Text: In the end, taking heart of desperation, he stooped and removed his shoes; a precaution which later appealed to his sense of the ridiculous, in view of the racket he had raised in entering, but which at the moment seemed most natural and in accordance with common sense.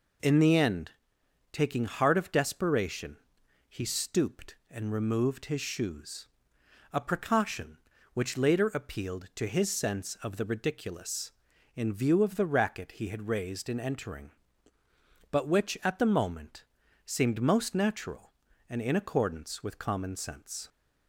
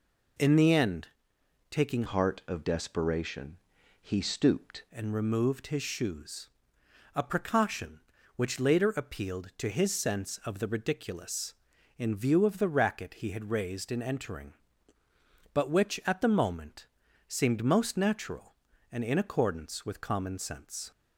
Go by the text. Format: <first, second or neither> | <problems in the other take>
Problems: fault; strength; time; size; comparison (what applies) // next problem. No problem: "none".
first | changes voice from "heart" to "stooped"; from 2.0 to 4.8 s; 2.8 s long // pauses between "moment" and "seemed"; at 16.8 s; 0.42 s long; also in the first